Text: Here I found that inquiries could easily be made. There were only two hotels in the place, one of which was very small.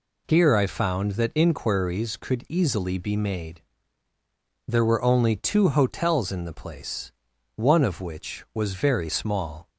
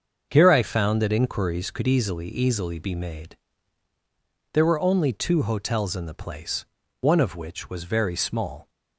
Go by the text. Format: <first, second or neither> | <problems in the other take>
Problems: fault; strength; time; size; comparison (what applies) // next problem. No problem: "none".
first | starts louder than the rest; until 1.3 s; 6.5 dB // says "easily" twice; at 2.2 s